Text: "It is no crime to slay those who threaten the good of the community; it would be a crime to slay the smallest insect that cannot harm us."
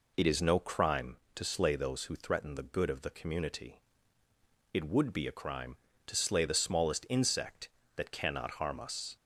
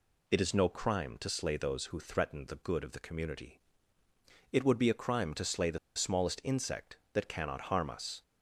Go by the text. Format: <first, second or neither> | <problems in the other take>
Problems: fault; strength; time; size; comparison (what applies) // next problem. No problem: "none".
first | pauses between "the" and "smallest"; slight; at 5.7 s; 0.17 s long